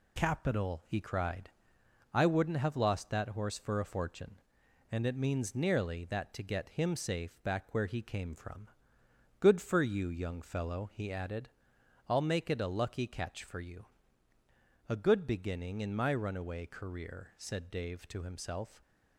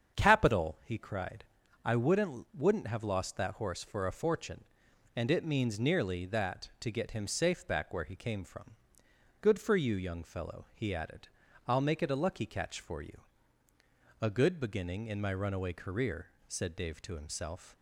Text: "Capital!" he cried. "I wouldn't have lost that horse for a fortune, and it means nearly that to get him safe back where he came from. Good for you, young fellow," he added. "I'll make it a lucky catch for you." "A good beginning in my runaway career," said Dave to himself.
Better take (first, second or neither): first